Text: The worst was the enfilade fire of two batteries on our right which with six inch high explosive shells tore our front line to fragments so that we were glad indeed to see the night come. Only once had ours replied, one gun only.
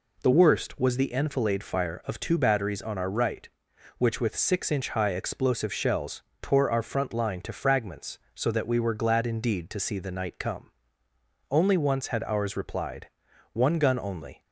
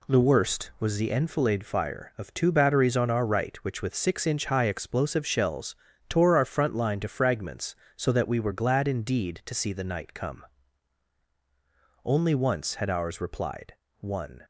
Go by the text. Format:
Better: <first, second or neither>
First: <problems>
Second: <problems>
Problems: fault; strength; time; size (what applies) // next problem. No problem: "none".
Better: first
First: pauses between "shells" and "tore"; slight; at 6.2 s; 0.20 s long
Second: pauses between "shells" and "tore"; slight; at 5.7 s; 0.32 s long // stops before "gun only"; at 14.4 s